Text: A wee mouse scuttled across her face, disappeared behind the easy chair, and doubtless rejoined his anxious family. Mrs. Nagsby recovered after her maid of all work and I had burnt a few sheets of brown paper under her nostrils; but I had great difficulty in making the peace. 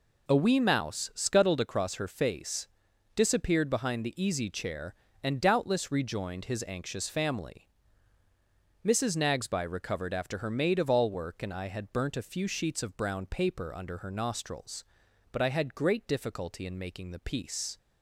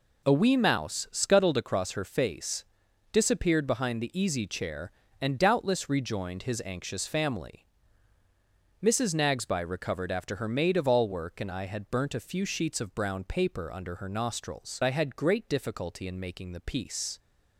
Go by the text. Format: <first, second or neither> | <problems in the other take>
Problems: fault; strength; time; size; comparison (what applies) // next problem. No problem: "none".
first | skips "but"; at 14.8 s